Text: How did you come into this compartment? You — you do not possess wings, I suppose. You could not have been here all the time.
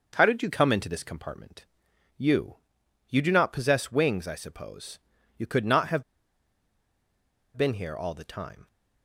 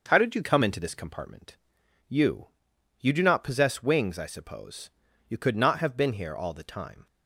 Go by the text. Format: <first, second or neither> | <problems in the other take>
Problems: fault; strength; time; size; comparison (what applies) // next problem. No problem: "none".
second | starts louder than the rest; noticeable; until 1.1 s; 6 dB // pauses between "have" and "been"; strong; at 6.0 s; 1.5 s long